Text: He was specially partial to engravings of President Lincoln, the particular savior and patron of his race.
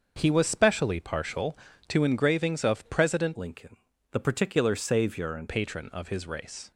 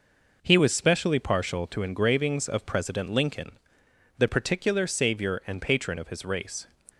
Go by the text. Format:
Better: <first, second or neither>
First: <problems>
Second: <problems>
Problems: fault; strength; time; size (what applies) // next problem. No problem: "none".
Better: second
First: starts louder than the rest; until 1.1 s; 6.5 dB // changes voice from "Lincoln" to "and"; from 3.3 to 5.4 s; 2.1 s long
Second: none